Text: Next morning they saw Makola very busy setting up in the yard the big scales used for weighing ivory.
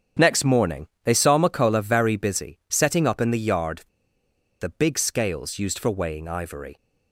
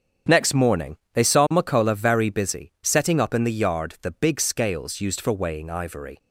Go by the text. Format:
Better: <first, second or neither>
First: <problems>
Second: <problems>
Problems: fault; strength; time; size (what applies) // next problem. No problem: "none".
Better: second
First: starts louder than the rest; strong; until 1.3 s; 8 dB // pauses between "morning" and "they"; slight; at 0.8 s; 0.16 s long // pauses between "yard" and "the"; noticeable; at 3.8 s; 0.79 s long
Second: starts louder than the rest; strong; until 1.4 s; 8 dB // pauses between "morning" and "they"; slight; at 0.9 s; 0.16 s long